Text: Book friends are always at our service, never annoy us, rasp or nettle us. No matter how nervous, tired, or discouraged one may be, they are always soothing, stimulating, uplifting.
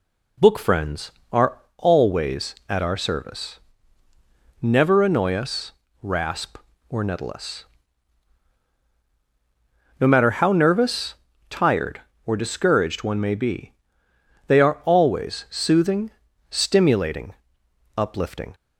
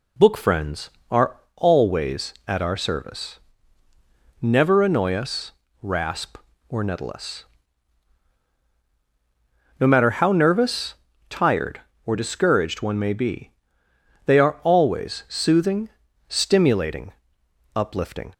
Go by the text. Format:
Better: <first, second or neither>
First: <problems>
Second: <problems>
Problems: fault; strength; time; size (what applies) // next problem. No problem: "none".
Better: neither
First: pauses between "are" and "always"; slight; at 1.5 s; 0.20 s long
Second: pauses between "are" and "always"; slight; at 1.3 s; 0.20 s long